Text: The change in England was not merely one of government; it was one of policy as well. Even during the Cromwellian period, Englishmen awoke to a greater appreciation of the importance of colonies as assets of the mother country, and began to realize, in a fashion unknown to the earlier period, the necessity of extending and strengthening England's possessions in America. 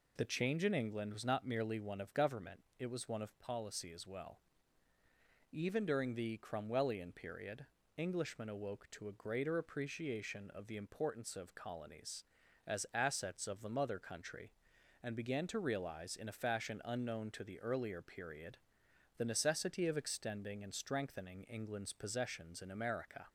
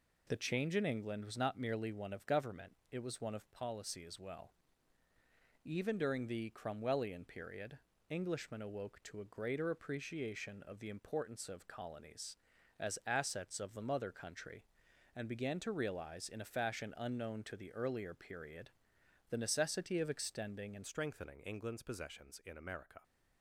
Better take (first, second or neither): first